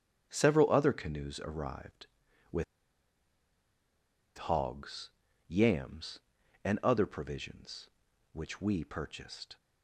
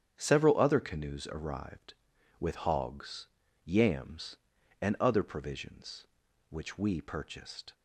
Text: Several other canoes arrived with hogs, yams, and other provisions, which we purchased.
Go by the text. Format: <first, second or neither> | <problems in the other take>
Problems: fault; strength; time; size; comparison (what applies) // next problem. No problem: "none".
second | starts louder than the rest; strong; until 1.3 s; 8 dB; strong in the second // pauses between "with" and "hogs"; strong; at 2.6 s; 1.7 s long